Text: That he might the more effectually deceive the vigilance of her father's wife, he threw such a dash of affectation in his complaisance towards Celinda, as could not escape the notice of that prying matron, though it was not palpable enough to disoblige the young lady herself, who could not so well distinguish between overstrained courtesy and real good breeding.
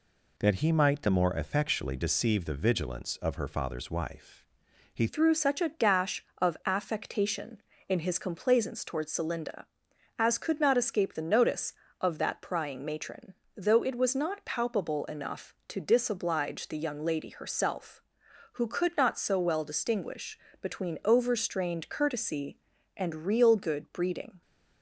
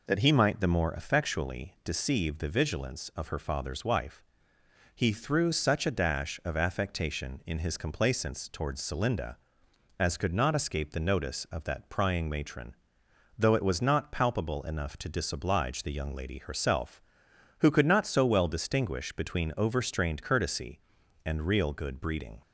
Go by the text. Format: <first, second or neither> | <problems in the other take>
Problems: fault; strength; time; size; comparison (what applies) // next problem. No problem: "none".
second | changes voice at "threw"; from 5.0 s on; 19.4 s long // pauses between "distinguish" and "between"; slight; at 20.3 s; 0.20 s long